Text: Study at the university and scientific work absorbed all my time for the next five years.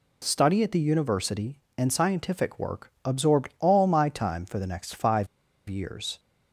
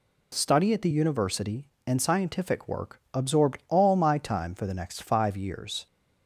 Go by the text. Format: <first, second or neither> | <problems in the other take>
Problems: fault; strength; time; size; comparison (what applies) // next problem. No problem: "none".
second | pauses between "five" and "years"; at 5.2 s; 0.42 s long